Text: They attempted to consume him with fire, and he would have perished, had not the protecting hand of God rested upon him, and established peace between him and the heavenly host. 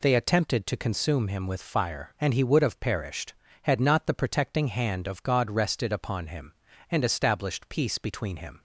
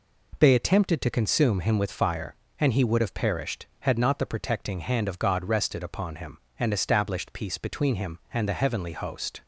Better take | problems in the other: second | stops before "and the heavenly host"; at 8.5 s

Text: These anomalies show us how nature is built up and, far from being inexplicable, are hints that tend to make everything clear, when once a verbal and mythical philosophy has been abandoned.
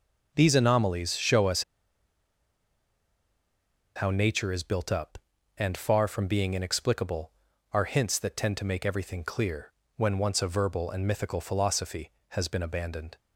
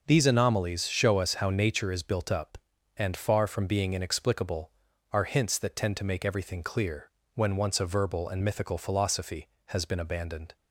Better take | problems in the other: second | pauses between "us" and "how"; strong; at 1.6 s; 2.3 s long

